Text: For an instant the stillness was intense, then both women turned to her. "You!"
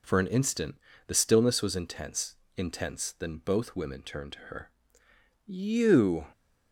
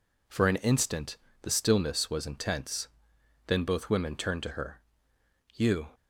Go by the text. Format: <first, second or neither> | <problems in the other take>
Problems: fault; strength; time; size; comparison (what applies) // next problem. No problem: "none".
second | pauses between "instant" and "the"; slight; at 0.7 s; 0.32 s long; slight in the second // says "intense" twice; at 2.5 s